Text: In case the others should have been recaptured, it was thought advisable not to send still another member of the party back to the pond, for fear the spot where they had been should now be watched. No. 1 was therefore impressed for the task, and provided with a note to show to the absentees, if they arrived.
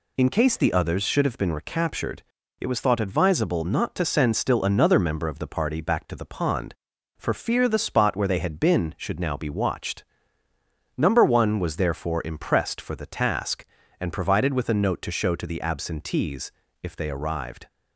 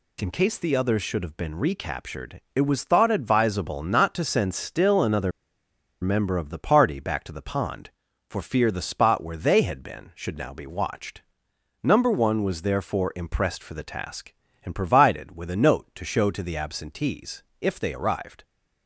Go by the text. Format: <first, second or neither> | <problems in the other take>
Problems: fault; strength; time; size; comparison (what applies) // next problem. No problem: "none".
first | pauses between "another" and "member"; noticeable; at 5.3 s; 0.70 s long